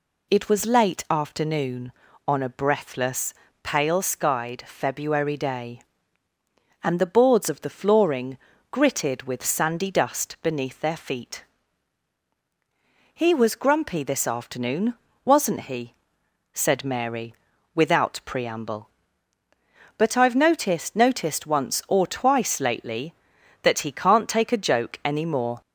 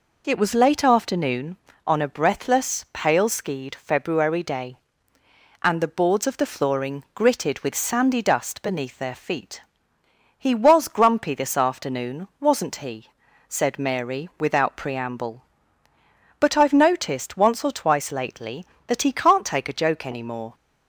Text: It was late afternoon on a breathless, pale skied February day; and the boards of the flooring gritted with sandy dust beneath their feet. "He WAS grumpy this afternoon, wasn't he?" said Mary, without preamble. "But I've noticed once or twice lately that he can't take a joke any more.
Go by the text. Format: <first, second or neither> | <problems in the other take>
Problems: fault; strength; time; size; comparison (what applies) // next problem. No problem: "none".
second | pauses between "flooring" and "gritted"; slight; at 8.3 s; 0.36 s long // says "noticed" twice; at 20.9 s